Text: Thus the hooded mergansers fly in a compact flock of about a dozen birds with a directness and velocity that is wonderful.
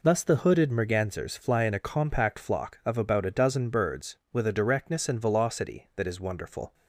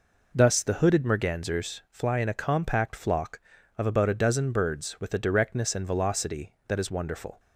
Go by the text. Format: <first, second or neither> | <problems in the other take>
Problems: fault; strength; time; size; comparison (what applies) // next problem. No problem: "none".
neither | none